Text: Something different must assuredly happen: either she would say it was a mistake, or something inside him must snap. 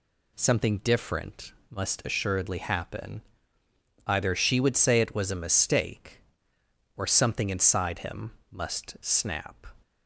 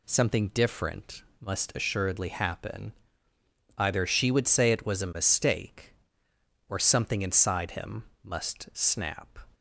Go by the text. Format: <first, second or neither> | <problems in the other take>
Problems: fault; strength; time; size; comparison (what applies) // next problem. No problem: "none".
neither | pauses between "different" and "must"; slight; the same in both // pauses between "him" and "must"; slight; the same in both